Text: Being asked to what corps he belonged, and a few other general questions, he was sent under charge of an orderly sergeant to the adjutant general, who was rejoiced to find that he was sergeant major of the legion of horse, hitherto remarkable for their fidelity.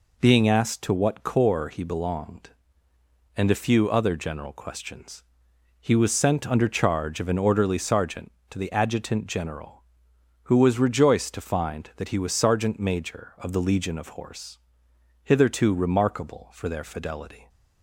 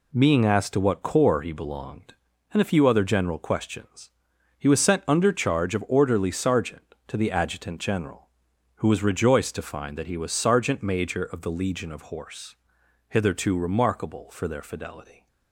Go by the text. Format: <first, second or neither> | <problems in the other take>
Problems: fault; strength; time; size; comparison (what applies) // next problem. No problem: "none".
first | skips "an"; at 5.8 s